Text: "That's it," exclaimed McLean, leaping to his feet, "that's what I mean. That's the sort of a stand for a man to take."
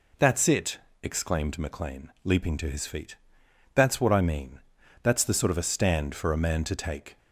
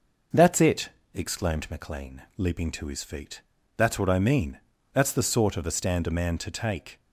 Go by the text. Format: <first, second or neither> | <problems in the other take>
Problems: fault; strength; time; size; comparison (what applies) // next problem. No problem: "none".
first | skips "for"; at 6.0 s